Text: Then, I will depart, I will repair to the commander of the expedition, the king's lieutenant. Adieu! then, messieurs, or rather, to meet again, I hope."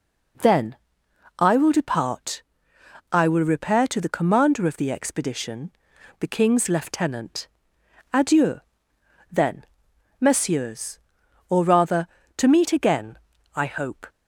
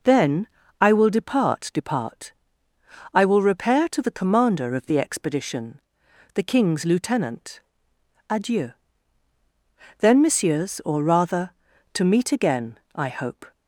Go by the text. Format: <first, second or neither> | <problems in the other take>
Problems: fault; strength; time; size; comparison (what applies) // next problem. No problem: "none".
first | says "depart" twice; at 1.7 s